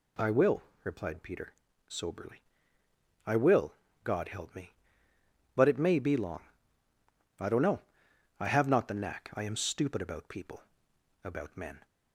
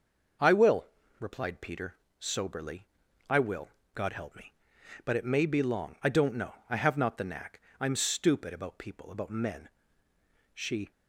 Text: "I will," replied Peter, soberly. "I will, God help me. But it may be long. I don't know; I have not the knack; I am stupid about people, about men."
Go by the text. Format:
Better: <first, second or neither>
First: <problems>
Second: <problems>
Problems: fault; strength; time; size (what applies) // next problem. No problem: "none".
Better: first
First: none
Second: goes on to say "She"; slight; from 10.5 s on; 0.38 s long